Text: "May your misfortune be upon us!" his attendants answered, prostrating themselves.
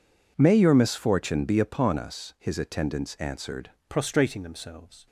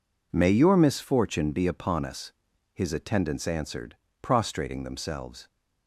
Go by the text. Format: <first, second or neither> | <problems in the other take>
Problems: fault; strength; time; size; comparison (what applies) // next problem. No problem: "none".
second | changes voice at "prostrating"; from 3.8 s on; 1.2 s long